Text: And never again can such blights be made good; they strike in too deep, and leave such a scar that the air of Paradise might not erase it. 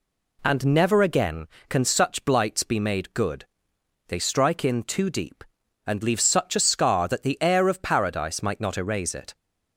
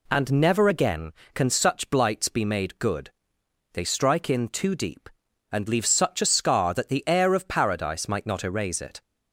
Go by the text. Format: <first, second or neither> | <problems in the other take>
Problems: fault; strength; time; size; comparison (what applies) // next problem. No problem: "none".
neither | none